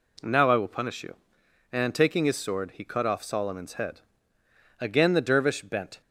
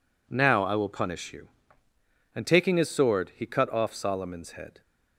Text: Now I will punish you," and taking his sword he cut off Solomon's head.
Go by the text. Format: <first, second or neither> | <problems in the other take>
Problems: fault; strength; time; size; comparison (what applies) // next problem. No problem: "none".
second | goes on to say "Again the Dervish bent"; noticeable; from 4.8 s on; 1.2 s long